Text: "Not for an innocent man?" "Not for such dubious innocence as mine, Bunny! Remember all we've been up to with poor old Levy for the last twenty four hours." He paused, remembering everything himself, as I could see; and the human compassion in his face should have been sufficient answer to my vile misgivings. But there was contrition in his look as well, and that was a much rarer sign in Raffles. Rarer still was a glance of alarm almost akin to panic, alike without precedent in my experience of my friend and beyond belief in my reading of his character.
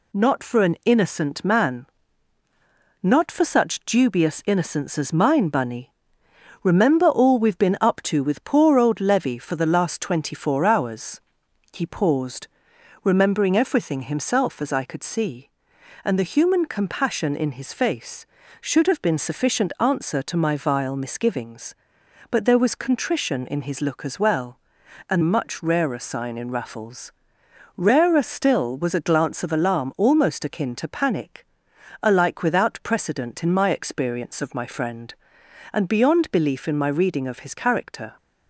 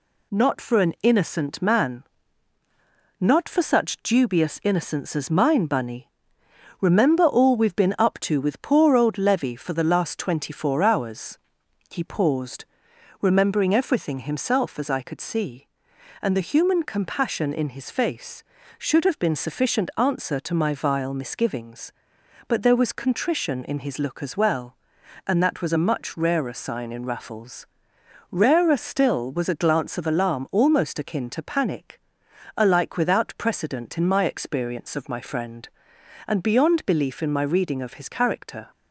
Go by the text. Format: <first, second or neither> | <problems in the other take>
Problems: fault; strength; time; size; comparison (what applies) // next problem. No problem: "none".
second | skips "that was a"; at 25.2 s